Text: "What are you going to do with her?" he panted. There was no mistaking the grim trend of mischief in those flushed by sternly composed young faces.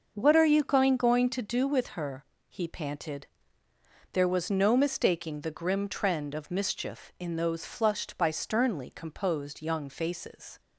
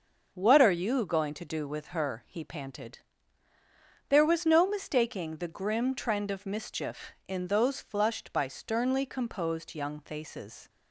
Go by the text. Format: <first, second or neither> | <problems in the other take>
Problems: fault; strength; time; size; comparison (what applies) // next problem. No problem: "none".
second | starts louder than the rest; until 1.1 s; 6 dB; noticeable in the second // says "going" twice; at 0.9 s